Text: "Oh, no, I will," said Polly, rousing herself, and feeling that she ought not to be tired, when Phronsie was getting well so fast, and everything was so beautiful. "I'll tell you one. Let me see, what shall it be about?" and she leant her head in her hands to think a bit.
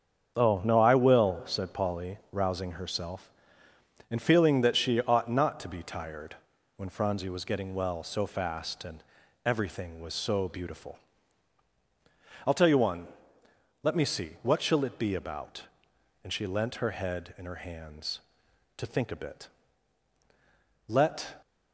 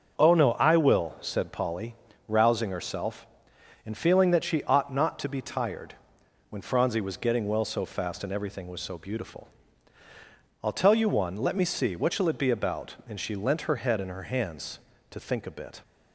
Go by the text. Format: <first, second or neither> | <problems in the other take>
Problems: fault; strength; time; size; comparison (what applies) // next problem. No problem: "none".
second | starts louder than the rest; until 1.3 s; 7 dB; noticeable in the second // pauses between "and" and "everything"; at 9.0 s; 0.42 s long // goes on to say "Let"; from 20.8 s on; 0.54 s long